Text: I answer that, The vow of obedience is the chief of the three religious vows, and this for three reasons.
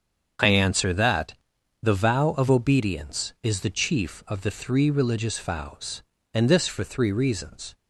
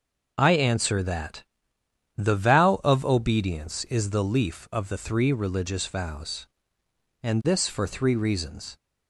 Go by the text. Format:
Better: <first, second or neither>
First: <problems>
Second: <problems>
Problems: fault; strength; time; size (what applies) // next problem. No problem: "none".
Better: first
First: starts louder than the rest; strong; until 1.8 s; 7 dB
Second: starts louder than the rest; noticeable; until 1.3 s; 6 dB // says "leaf" for "chief"; at 4.2 s